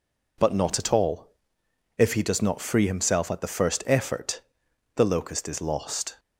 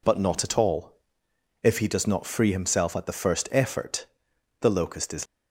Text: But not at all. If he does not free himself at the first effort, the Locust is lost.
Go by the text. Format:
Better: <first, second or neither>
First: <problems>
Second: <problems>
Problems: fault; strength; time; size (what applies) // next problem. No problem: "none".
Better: first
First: none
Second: stops before "lost"; at 5.2 s